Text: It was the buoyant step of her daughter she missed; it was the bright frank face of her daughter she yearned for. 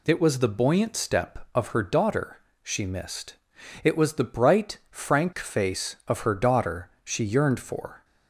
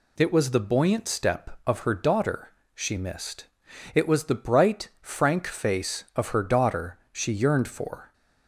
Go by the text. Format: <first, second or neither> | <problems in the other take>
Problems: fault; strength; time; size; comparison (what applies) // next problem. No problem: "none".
neither | pauses between "daughter" and "she"; slight; the same in both